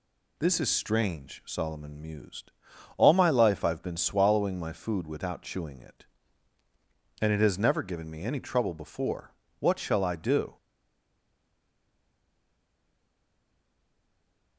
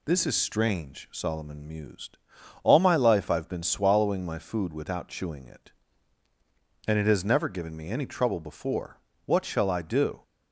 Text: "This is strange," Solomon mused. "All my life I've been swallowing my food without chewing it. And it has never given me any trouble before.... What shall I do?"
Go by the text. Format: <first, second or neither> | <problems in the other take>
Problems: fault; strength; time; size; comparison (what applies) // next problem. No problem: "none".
second | stays silent after the last word; strong; from 10.5 s on; 4.0 s long